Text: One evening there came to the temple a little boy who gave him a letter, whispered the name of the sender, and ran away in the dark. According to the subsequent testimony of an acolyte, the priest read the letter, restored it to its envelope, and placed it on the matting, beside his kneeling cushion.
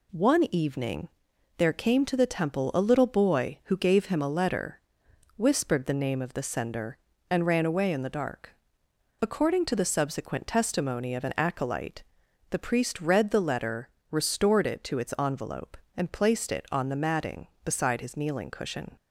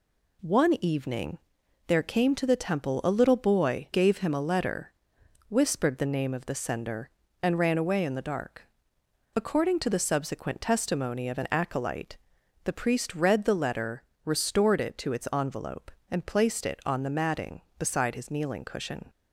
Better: first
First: pauses between "evening" and "there"; noticeable; at 1.0 s; 0.50 s long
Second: pauses between "evening" and "there"; noticeable; at 1.3 s; 0.50 s long // skips "who"; at 3.9 s

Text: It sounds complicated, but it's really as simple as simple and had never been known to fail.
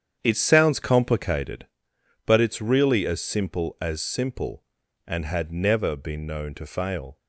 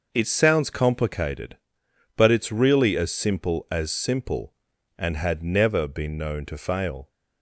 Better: second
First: starts louder than the rest; strong; until 1.7 s; 8.5 dB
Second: none

